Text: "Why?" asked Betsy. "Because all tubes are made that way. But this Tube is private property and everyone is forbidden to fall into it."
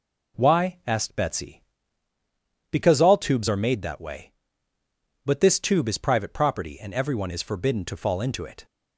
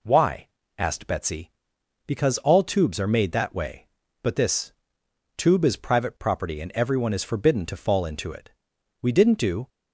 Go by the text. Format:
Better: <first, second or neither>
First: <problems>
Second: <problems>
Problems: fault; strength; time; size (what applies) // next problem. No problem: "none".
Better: first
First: none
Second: pauses between "this" and "Tube"; noticeable; at 4.7 s; 0.64 s long // goes on to say "We didn't do"; noticeable; from 9.0 s on; 0.68 s long